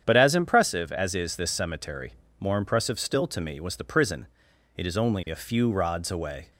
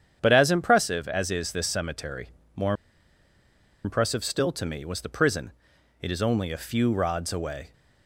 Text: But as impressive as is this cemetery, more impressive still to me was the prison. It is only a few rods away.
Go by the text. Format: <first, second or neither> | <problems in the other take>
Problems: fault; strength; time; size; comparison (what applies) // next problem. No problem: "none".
first | starts louder than the rest; strong; until 1.2 s; 8.5 dB; strong in the first // pauses between "more" and "impressive"; at 2.7 s; 1.1 s long